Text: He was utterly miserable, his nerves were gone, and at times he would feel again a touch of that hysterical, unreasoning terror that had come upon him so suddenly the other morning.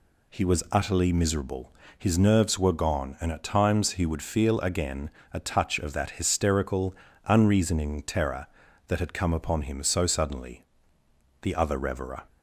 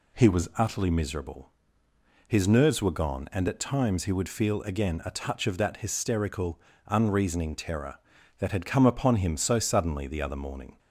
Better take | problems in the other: second | pauses between "again" and "a"; slight; at 5.0 s; 0.24 s long // pauses between "suddenly" and "the"; noticeable; at 10.6 s; 0.80 s long // says "reverer" for "morning"; at 11.7 s

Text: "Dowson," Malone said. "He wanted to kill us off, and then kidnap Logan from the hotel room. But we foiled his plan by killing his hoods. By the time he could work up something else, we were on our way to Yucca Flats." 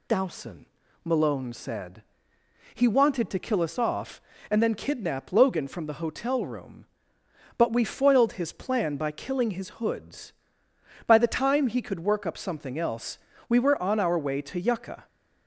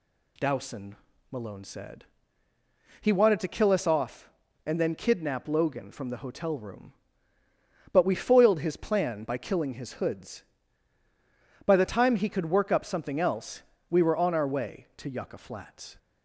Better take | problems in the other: second | stops before "Flats"; at 15.0 s

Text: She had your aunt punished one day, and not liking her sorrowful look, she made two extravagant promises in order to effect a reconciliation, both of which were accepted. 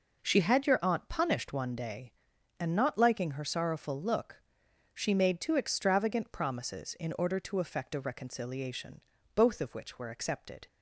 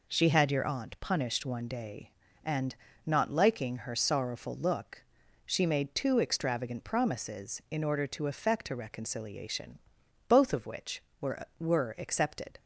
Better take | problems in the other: first | pauses between "and" and "not"; slight; at 2.7 s; 0.30 s long // says "were" twice; at 11.5 s

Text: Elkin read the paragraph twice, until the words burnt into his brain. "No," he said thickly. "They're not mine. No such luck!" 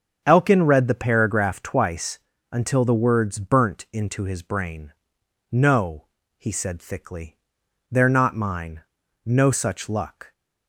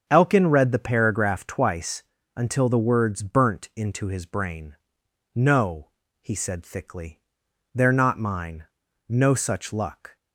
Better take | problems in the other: neither | starts louder than the rest; strong; the same in both

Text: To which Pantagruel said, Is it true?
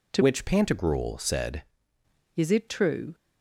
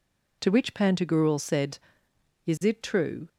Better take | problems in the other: second | changes voice from "which" to "said"; from 0.2 to 1.6 s; 1.4 s long

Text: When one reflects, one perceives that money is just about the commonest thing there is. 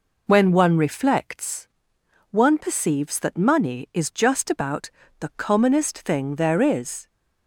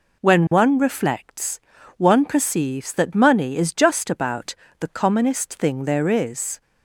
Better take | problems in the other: neither | pauses between "about" and "the"; slight; the same in both

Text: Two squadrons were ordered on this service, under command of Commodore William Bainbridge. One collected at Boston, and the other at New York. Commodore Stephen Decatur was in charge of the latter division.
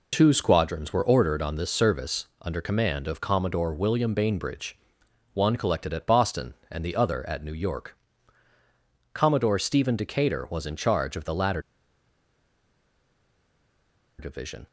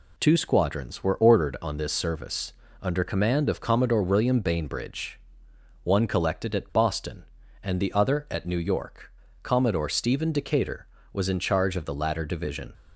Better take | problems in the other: second | pauses between "latter" and "division"; strong; at 11.6 s; 2.5 s long

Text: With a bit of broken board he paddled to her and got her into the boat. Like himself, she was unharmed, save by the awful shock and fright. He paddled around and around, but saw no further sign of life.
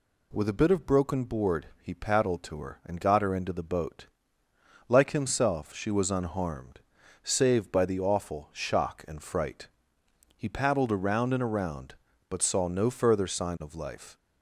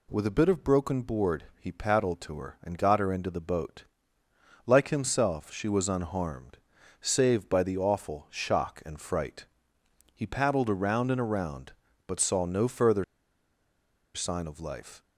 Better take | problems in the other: first | pauses between "board" and "he"; slight; at 1.4 s; 0.16 s long; slight in the first // pauses between "further" and "sign"; at 13.0 s; 1.1 s long

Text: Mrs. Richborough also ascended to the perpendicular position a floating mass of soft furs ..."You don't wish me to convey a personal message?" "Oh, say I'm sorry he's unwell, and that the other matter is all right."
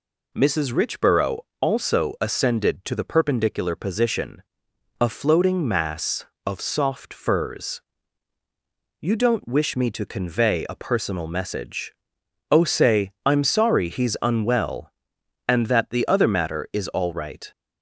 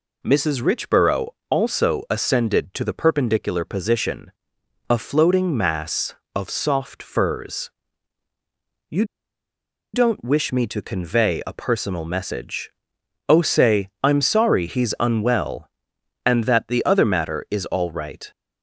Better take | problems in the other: first | pauses between "Richborough" and "also"; slight; at 1.2 s; 0.20 s long; slight in the first // pauses between "position" and "a"; noticeable; at 4.3 s; 0.56 s long; noticeable in the first // pauses between "You" and "don't"; noticeable; at 9.0 s; 0.90 s long

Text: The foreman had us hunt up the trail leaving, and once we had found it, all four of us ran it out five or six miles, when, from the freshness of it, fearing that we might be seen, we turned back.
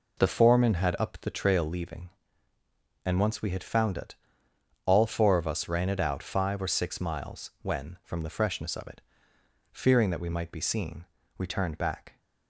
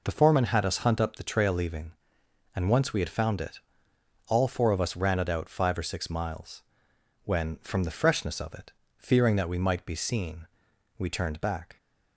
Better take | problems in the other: second | skips "us hunt"; at 0.9 s

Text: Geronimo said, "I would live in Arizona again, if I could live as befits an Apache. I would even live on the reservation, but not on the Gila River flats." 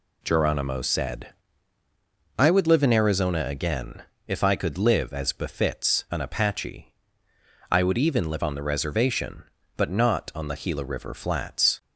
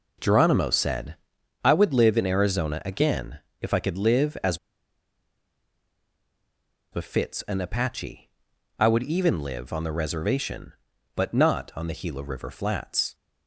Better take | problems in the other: first | pauses between "as" and "befits"; strong; at 4.5 s; 2.3 s long

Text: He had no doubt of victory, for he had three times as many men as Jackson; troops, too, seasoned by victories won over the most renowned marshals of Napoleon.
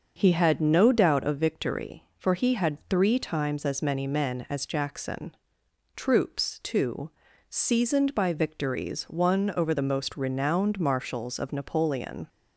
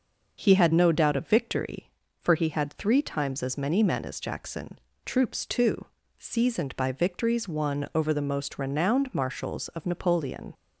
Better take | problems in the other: neither | starts louder than the rest; the same in both

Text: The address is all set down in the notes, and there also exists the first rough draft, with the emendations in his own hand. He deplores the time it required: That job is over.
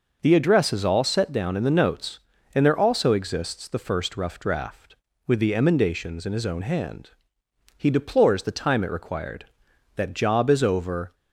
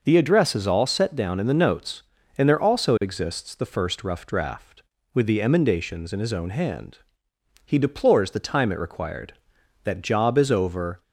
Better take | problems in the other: neither | none

